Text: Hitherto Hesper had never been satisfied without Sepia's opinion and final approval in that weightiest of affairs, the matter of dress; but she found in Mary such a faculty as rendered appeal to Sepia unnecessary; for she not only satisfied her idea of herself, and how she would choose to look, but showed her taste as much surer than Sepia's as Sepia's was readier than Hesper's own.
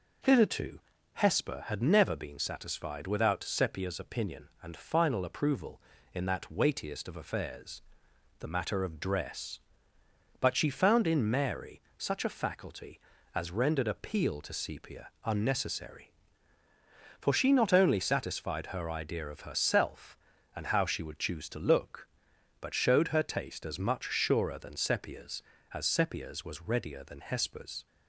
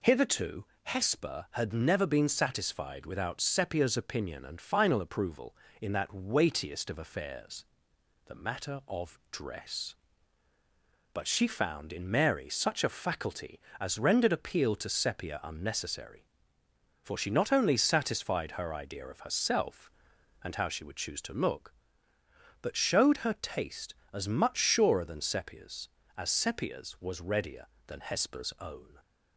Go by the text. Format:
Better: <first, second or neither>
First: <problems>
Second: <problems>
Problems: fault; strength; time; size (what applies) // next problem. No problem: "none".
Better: second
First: pauses between "Hitherto" and "Hesper"; slight; at 0.7 s; 0.36 s long // pauses between "Mary" and "such"; slight; at 11.8 s; 0.16 s long // pauses between "Sepia" and "unnecessary"; slight; at 15.0 s; 0.16 s long // stops before "own"; at 27.8 s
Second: pauses between "Hitherto" and "Hesper"; slight; at 0.6 s; 0.18 s long